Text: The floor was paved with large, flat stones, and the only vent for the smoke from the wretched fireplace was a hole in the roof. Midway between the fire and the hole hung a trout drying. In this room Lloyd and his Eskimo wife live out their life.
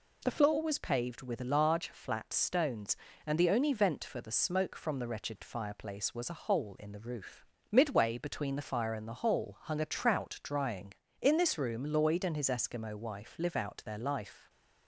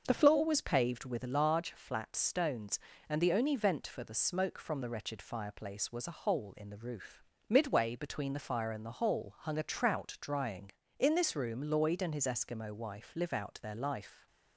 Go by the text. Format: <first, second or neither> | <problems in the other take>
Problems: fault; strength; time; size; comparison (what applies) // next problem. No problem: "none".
first | starts louder than the rest; until 1.2 s; 6 dB